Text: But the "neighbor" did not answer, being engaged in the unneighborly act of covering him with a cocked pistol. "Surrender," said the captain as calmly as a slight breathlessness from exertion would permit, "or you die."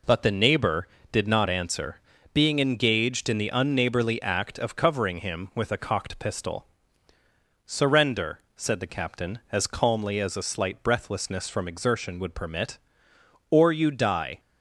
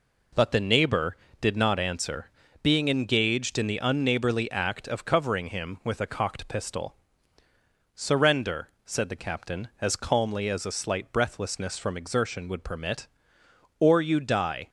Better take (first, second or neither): neither